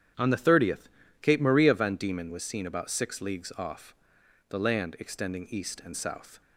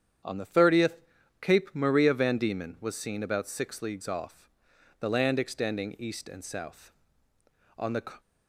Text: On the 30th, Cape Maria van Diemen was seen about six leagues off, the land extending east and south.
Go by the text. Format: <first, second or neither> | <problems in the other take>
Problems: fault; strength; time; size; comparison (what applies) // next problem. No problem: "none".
first | starts louder than the rest; strong; until 1.6 s; 8.5 dB; strong in the first // goes on to say "On the"; slight; from 7.7 s on; 0.42 s long